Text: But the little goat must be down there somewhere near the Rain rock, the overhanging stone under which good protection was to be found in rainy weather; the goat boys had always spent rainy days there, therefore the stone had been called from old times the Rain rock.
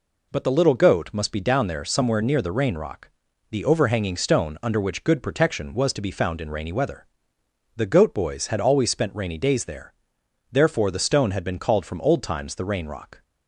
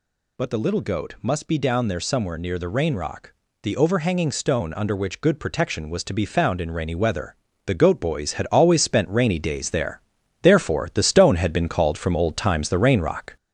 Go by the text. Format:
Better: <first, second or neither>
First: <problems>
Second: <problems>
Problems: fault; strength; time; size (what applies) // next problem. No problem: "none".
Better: first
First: none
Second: gets louder; noticeable; throughout; 4.5 dB